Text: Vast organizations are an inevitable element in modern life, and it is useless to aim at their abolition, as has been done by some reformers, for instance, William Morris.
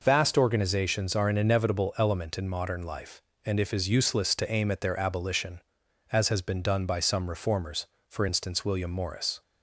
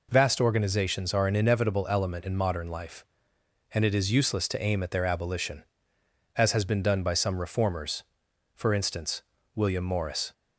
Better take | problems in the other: second | says "if" for "it"; at 3.6 s

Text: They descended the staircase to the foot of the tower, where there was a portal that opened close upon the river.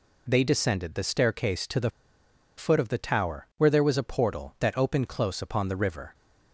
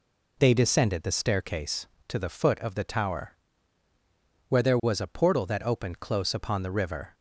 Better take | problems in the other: second | pauses between "the" and "foot"; noticeable; at 1.8 s; 0.68 s long

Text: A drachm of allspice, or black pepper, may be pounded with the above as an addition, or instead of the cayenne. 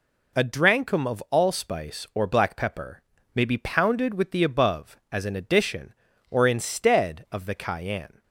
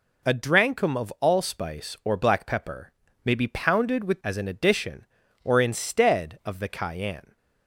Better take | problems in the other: first | skips "the above"; at 4.2 s

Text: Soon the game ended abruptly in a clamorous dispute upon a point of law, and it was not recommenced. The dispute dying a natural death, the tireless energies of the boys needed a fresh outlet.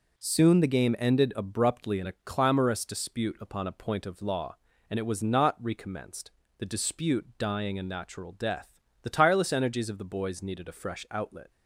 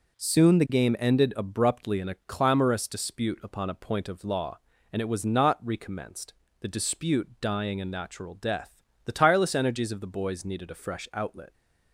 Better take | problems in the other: neither | none

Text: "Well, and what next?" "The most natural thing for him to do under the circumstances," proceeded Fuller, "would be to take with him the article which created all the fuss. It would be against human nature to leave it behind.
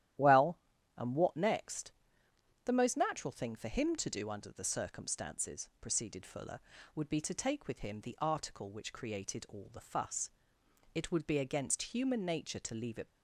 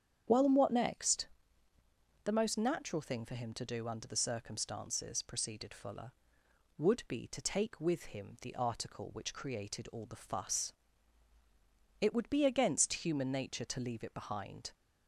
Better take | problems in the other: second | starts louder than the rest; strong; until 1.5 s; 12.5 dB; strong in the second // stops before "behind"; at 13.0 s

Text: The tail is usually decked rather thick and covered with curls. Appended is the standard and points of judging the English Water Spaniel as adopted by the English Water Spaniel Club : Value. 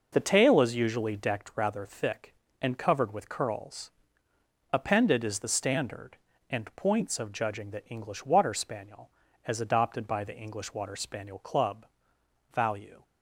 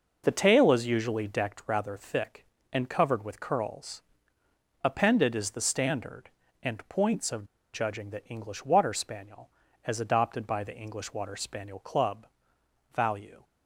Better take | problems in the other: first | pauses between "of" and "judging"; slight; at 7.4 s; 0.28 s long

